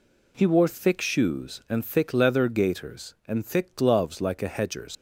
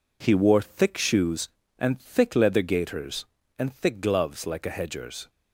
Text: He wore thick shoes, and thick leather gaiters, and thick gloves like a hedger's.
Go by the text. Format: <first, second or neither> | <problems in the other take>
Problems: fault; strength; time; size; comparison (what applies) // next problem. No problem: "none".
second | leaves "hedger's" unfinished; at 4.9 s; 125 ms